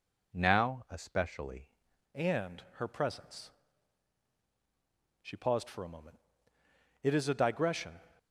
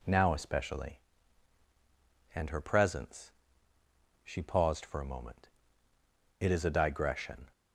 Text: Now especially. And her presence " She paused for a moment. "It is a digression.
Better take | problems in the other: second | changes voice at "And"; from 2.1 s on; 5.9 s long

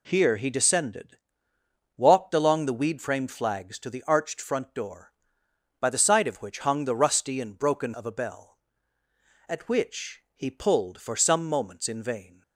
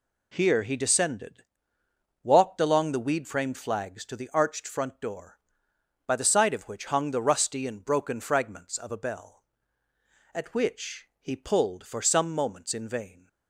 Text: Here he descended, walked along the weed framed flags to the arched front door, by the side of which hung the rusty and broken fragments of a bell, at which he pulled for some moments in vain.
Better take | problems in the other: second | skips "fragments"; at 7.9 s

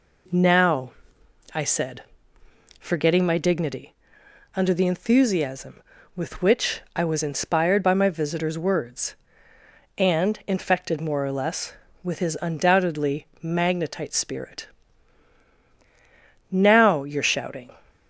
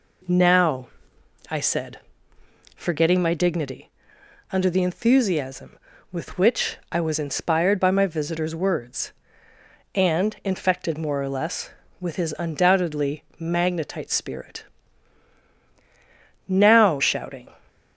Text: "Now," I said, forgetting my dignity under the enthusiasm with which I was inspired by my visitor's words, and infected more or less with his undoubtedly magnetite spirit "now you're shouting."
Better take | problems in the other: first | pauses between "dignity" and "under"; noticeable; at 3.9 s; 0.62 s long; noticeable in the first // pauses between "which" and "I"; slight; at 6.7 s; 0.16 s long; slight in the first // pauses between "spirit" and "now"; strong; at 14.6 s; 1.8 s long; strong in the first // skips "you're"; at 17.0 s

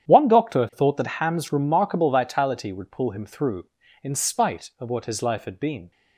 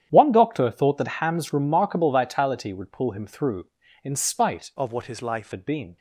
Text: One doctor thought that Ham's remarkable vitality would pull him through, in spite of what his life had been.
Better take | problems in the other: first | starts louder than the rest; strong; until 1.1 s; 10 dB; strong in the first // changes voice from "of" to "life"; from 4.7 to 5.5 s; 0.8 s long

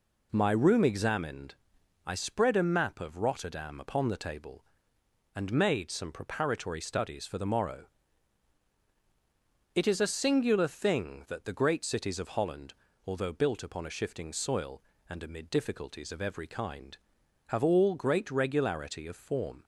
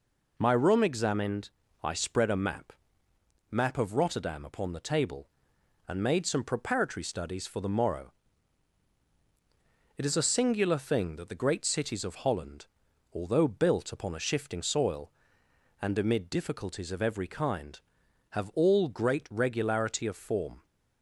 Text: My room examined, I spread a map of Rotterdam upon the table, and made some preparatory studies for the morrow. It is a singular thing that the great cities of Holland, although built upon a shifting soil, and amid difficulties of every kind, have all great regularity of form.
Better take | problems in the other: first | says "map" twice; at 3.5 s

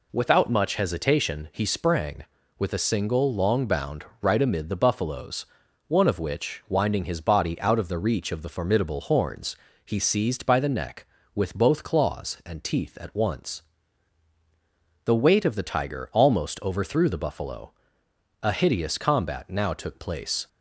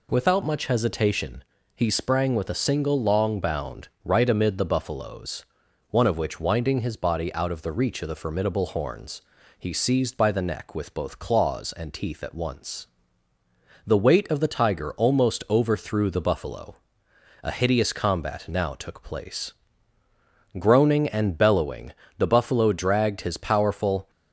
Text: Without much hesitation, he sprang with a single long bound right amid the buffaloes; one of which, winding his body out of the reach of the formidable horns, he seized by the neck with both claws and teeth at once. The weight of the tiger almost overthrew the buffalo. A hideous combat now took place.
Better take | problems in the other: first | pauses between "bound" and "right"; slight; at 3.8 s; 0.16 s long; slight in the first // goes on to say "Groaning and bellowing the buffalo dragged his powerful"; strong; from 20.5 s on; 3.5 s long

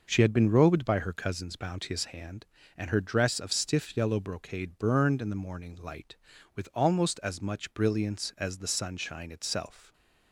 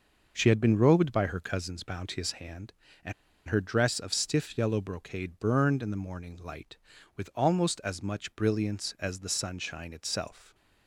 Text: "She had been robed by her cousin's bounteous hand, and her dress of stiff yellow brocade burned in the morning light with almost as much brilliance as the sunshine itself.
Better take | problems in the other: first | pauses between "and" and "her"; slight; at 3.1 s; 0.35 s long

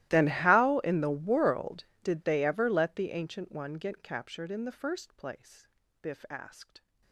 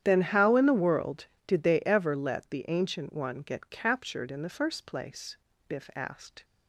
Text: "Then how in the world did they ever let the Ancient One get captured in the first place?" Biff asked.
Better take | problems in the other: second | gets quieter; strong; throughout; 28.5 dB // starts louder than the rest; strong; until 1.1 s; 15.5 dB; strong in the second

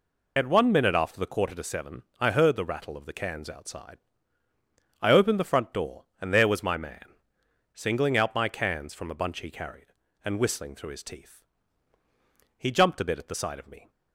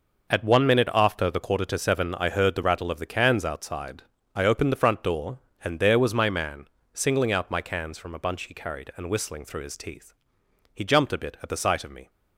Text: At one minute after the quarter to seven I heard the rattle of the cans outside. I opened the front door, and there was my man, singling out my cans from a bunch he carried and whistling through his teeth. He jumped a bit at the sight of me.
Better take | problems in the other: second | loses the start of "At"; at 0.3 s; 25 ms // pauses between "seven" and "I"; slight; at 2.0 s; 0.17 s long

